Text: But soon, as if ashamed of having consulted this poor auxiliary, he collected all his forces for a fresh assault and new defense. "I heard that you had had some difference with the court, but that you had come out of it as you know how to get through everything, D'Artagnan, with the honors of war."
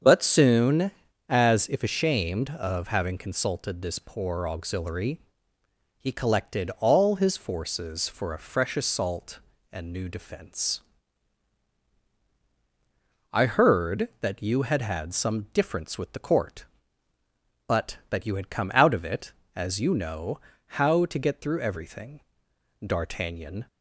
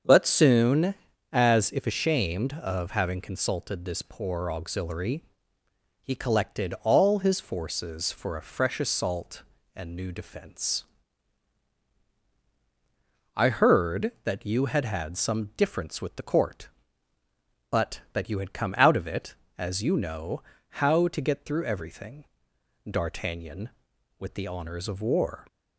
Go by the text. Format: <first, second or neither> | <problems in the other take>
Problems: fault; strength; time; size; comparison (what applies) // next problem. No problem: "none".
second | starts louder than the rest; strong; until 1.4 s; 7 dB; also in the second // pauses between "know" and "how"; at 20.4 s; 0.38 s long; also in the second // stops before "with the honors of war"; at 23.6 s